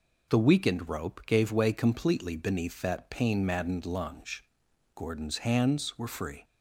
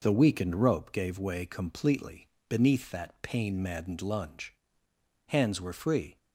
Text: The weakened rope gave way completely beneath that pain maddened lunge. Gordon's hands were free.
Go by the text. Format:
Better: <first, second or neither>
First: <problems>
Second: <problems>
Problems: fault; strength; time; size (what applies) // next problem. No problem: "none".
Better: first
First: none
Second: pauses between "completely" and "beneath"; slight; at 2.2 s; 0.22 s long // skips "Gordon's"; at 4.8 s